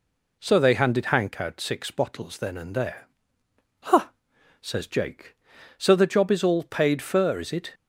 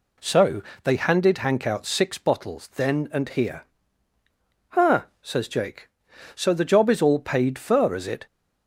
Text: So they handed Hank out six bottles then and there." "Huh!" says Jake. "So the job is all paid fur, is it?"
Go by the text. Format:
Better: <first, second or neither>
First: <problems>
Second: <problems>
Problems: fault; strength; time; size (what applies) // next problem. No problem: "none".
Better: first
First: none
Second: pauses between "So" and "they"; slight; at 0.6 s; 0.22 s long // says "here" for "there"; at 3.2 s